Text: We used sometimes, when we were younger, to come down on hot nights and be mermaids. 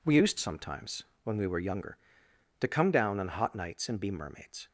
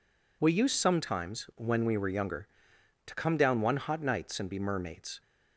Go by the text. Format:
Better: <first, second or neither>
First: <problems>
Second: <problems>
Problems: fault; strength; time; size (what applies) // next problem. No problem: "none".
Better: first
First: none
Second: says "one" for "on"; at 3.6 s